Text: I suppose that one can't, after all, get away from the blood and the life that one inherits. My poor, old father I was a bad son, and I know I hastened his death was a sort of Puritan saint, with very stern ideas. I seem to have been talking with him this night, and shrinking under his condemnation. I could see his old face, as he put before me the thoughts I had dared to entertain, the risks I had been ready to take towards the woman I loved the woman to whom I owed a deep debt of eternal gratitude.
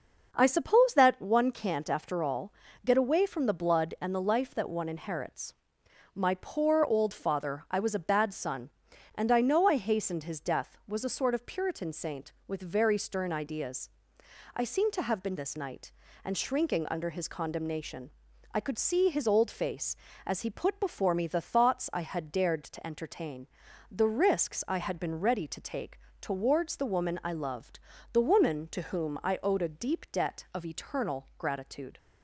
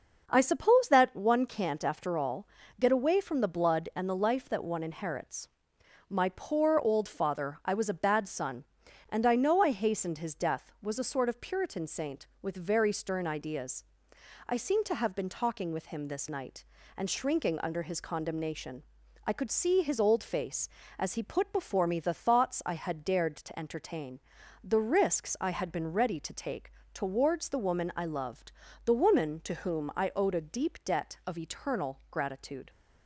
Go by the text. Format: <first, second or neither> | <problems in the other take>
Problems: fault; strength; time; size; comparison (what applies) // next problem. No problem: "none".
second | skips "talking with him"; at 15.3 s // pauses between "take" and "towards"; slight; at 25.9 s; 0.22 s long; slight in the second // pauses between "loved" and "the"; slight; at 27.7 s; 0.34 s long; slight in the second